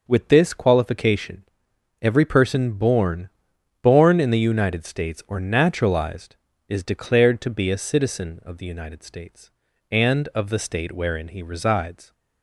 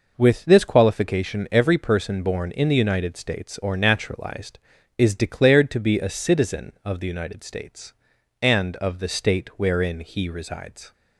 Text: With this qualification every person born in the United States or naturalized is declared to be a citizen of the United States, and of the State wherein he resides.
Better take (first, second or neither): second